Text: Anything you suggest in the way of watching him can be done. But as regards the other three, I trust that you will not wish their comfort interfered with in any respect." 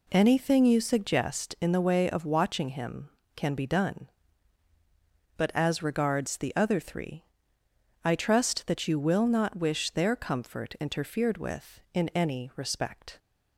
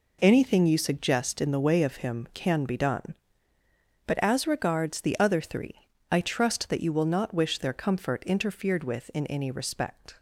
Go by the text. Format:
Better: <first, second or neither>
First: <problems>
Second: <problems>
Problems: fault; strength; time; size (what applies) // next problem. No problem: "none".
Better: first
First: none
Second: skips "watching"; at 1.9 s